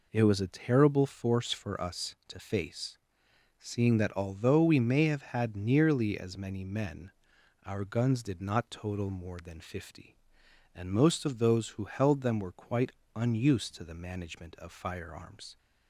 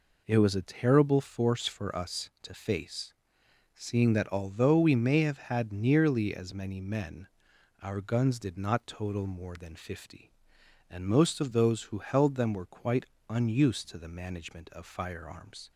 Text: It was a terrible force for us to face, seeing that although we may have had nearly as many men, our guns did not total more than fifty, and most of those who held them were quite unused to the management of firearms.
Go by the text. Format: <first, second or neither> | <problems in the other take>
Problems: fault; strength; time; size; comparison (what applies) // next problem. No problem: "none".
neither | pauses between "quite" and "unused"; slight; the same in both